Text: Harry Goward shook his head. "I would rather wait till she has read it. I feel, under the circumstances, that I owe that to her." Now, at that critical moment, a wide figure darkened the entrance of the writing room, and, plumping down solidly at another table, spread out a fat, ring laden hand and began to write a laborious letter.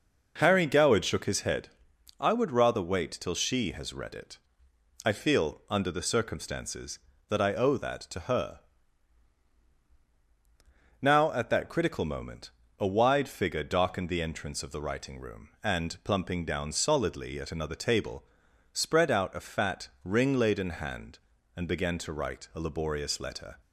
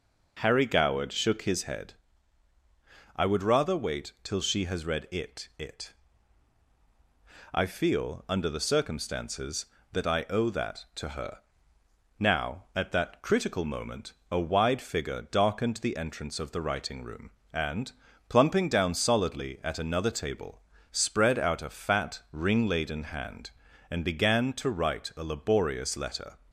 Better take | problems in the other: first | says "it" twice; at 5.5 s

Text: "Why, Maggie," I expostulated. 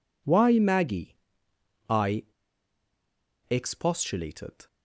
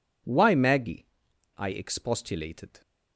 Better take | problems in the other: second | pauses between "I" and "expostulated"; strong; at 2.2 s; 1.2 s long

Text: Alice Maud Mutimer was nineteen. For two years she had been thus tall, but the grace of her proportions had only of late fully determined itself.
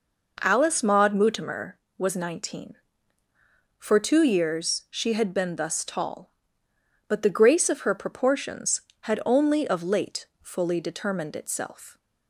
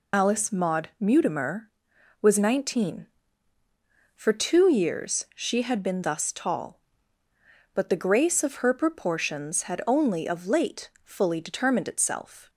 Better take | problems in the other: first | loses the start of "Alice"; at 0.1 s; 55 ms // pauses between "late" and "fully"; slight; at 10.8 s; 0.16 s long; slight in the first

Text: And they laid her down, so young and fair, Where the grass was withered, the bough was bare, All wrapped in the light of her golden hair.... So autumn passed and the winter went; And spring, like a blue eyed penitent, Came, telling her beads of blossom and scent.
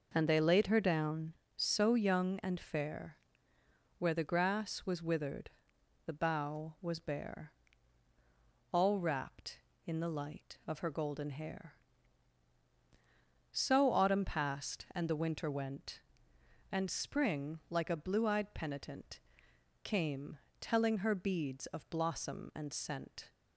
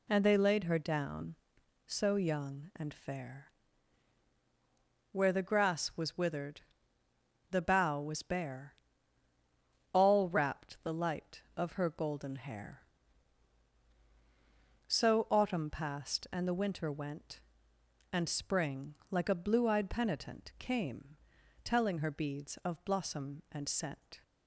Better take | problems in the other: first | skips "in"; at 10.8 s

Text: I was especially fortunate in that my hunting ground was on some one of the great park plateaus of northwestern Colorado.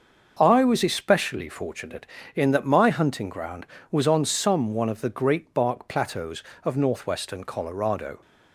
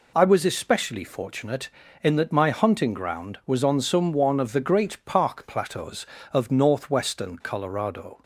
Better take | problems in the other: second | starts louder than the rest; until 1.4 s; 6.5 dB // says "bark" for "park"; at 5.5 s

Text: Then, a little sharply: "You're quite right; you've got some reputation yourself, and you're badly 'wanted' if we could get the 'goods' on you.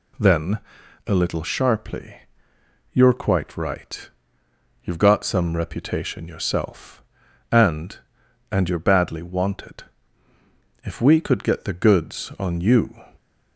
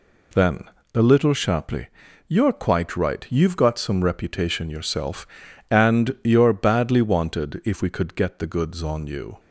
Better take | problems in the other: second | says "and" twice; at 8.4 s // pauses between "wanted" and "if"; at 9.8 s; 1.0 s long

